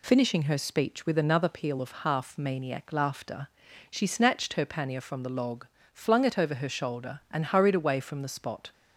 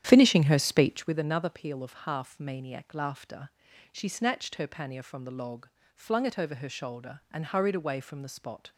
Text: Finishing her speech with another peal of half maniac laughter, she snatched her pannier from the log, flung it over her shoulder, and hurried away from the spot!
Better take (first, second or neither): first